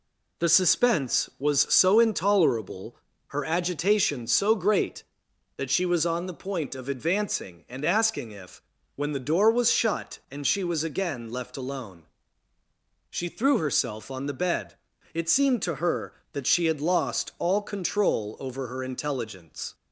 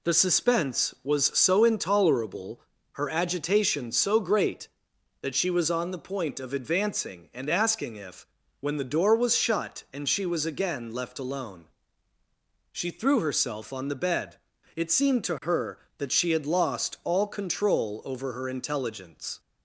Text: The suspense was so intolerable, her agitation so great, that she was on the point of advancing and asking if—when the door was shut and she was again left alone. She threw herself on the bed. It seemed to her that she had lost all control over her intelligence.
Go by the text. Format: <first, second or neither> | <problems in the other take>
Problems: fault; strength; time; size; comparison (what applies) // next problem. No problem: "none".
neither | none